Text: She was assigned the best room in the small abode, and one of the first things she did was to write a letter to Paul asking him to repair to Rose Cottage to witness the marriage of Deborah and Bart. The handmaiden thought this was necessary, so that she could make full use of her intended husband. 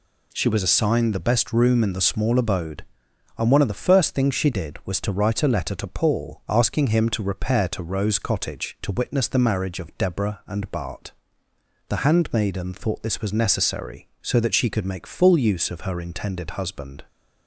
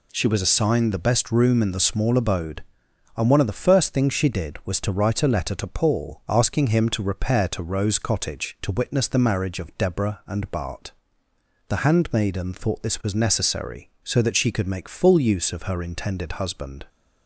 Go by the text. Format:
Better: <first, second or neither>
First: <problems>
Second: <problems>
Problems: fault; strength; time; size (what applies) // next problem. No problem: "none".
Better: neither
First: none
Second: none